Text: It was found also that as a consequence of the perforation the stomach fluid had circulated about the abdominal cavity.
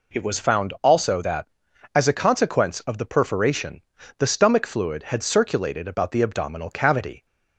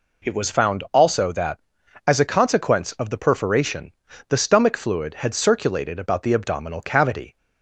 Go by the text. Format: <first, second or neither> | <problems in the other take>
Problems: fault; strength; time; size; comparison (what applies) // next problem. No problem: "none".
neither | pauses between "perforation" and "the"; the same in both